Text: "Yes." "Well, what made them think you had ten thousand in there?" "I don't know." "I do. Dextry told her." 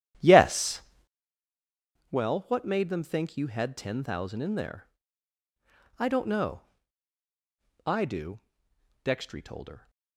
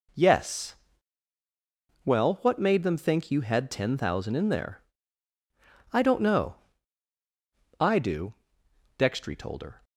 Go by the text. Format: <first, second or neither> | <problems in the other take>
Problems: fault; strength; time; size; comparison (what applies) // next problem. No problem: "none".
second | starts louder than the rest; strong; until 1.3 s; 11 dB